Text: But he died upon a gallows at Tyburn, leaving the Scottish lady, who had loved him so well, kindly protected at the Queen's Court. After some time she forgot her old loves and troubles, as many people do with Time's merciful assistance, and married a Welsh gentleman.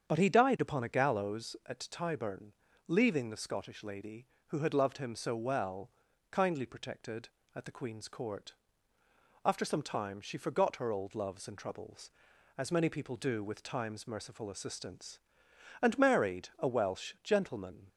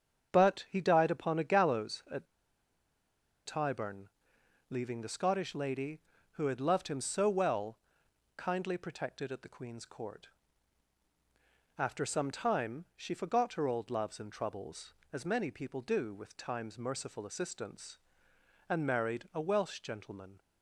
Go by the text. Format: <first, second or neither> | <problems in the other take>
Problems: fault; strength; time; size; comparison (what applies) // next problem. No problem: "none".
first | starts louder than the rest; strong; until 1.3 s; 7 dB; strong in the first // pauses between "at" and "Tyburn"; at 2.2 s; 1.2 s long